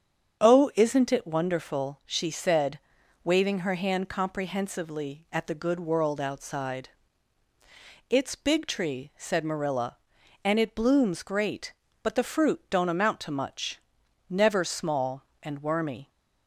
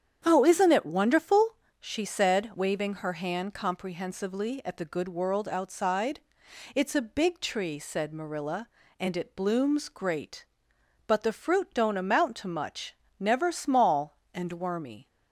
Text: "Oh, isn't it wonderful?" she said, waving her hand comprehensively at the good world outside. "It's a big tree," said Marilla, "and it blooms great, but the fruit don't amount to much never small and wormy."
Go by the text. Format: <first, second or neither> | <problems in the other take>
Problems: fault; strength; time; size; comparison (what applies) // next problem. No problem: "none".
second | starts louder than the rest; strong; until 1.4 s; 7.5 dB; strong in the second // skips "a"; at 8.3 s // pauses between "much" and "never"; noticeable; at 13.7 s; 0.48 s long; slight in the second